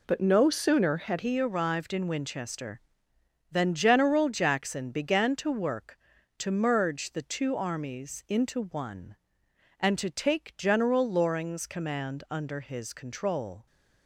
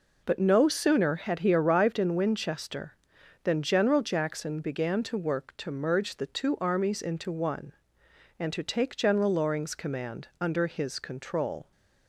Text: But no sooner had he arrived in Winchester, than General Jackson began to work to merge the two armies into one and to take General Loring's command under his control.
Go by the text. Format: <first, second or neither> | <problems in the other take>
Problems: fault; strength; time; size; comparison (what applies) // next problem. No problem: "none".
second | changes voice at "he"; from 1.1 s on; 12.5 s long